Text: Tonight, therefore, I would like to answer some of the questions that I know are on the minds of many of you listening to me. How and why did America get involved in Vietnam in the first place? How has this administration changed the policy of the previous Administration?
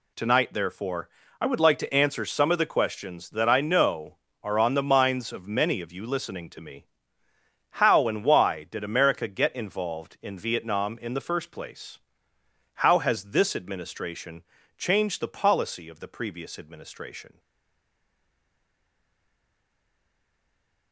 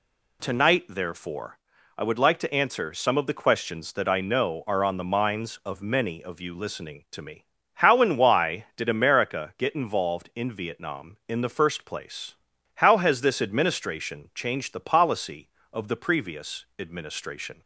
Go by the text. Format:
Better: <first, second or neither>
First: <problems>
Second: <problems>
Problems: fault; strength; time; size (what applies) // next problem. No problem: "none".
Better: second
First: pauses between "administration" and "changed"; slight; at 14.4 s; 0.34 s long // stays silent after the last word; strong; from 17.3 s on; 3.6 s long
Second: none